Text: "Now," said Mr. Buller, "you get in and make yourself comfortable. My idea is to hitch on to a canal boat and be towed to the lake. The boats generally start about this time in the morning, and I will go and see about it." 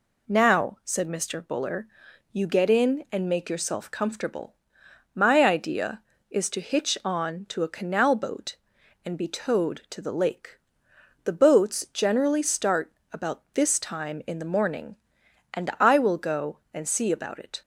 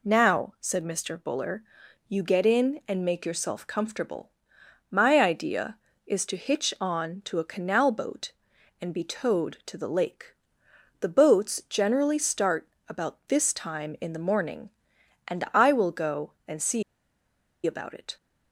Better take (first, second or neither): first